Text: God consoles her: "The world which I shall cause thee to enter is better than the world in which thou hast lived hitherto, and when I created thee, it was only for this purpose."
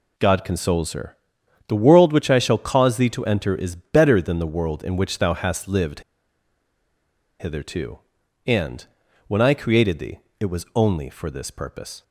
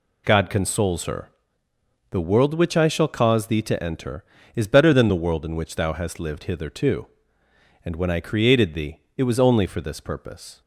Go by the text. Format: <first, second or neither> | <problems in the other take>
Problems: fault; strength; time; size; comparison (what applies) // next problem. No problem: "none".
second | pauses between "lived" and "hitherto"; strong; at 6.0 s; 1.3 s long // pauses between "and" and "when"; at 8.8 s; 0.40 s long